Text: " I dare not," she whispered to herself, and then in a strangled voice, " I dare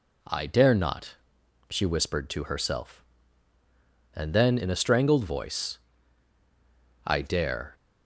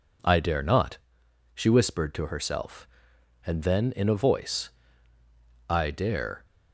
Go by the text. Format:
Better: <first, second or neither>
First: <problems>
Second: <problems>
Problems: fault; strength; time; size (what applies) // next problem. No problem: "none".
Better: first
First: none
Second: skips "strangled"; at 4.1 s